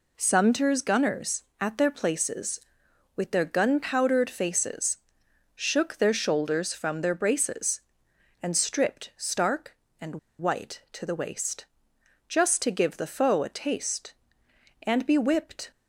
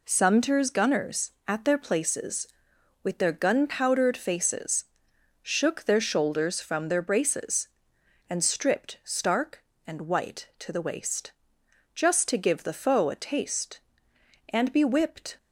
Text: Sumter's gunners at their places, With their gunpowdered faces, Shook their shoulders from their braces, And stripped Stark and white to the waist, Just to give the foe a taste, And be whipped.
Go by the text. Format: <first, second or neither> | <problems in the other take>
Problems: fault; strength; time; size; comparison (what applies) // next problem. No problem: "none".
second | pauses between "and" and "white"; slight; at 10.1 s; 0.22 s long